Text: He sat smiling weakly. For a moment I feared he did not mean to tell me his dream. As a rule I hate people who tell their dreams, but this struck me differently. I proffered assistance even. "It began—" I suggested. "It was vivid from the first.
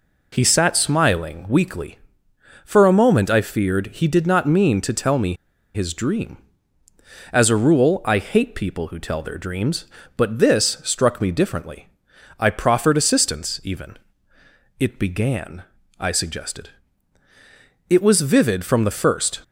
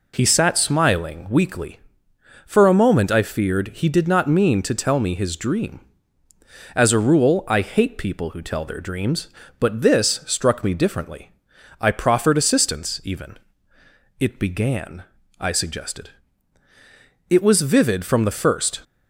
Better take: second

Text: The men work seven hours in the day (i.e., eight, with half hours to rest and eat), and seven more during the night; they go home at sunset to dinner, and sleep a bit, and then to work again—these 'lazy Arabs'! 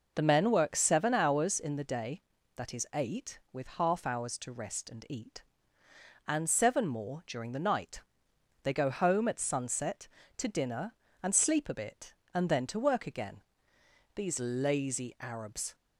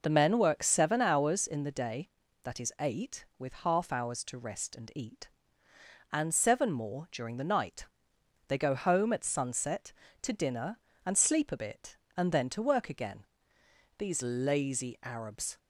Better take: neither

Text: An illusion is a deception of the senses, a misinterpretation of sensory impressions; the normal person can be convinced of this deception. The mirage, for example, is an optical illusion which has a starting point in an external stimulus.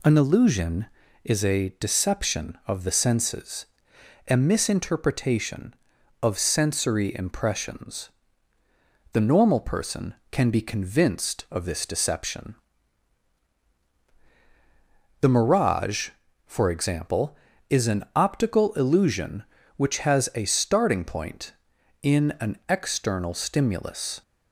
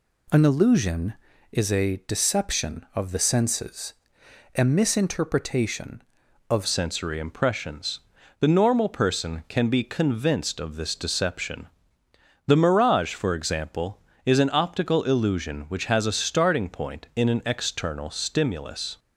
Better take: first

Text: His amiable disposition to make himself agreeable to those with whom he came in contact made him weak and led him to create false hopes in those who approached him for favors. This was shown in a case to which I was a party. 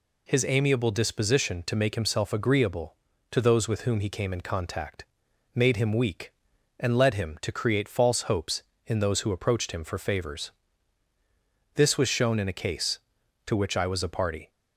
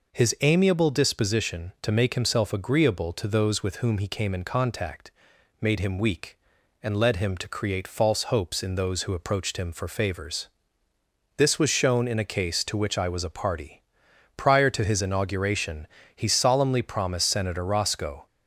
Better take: first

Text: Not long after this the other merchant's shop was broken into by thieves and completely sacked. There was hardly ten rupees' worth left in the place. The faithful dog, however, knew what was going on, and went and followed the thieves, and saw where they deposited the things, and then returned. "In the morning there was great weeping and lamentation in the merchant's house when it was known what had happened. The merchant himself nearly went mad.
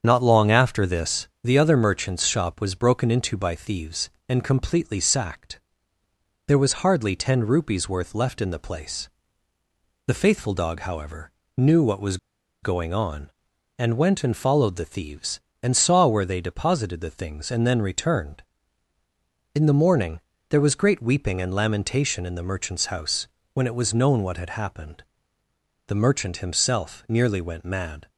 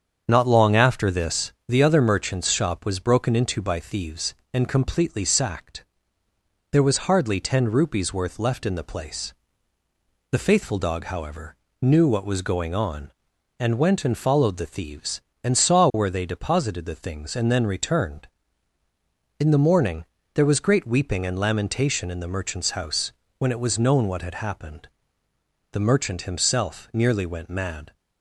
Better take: second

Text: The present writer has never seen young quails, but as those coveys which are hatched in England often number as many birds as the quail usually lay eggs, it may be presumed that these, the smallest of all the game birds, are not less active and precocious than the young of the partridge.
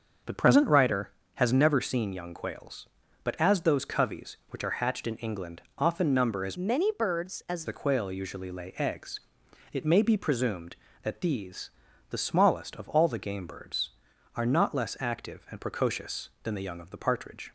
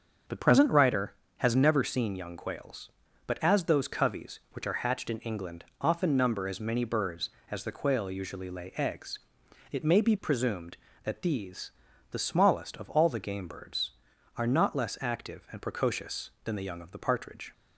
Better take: second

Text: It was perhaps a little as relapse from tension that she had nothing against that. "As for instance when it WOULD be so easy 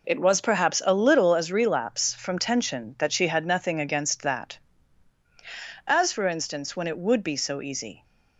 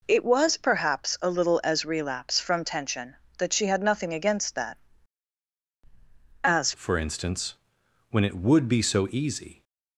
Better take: first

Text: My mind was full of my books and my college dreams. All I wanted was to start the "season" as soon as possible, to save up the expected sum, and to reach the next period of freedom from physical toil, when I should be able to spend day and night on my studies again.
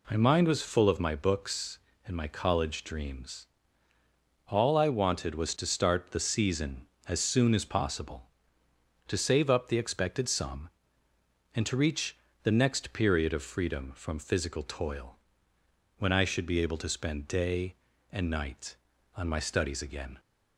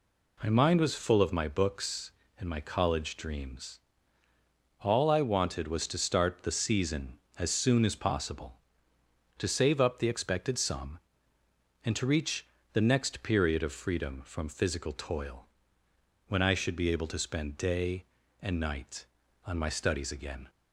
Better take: neither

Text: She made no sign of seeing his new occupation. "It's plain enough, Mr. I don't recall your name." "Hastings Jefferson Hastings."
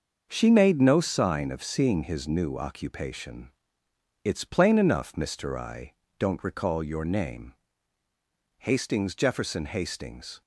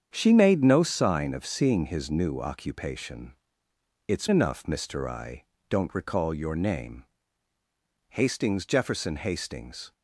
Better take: first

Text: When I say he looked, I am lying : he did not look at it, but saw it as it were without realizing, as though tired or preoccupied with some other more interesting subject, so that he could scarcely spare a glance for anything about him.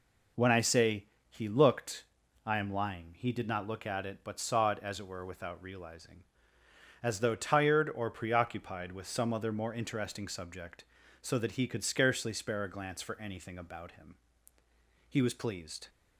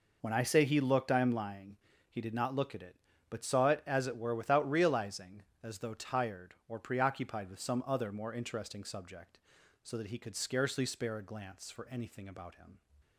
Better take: second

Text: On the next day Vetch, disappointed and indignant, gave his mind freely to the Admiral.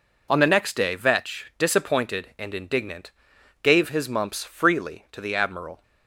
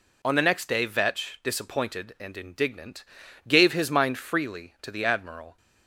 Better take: second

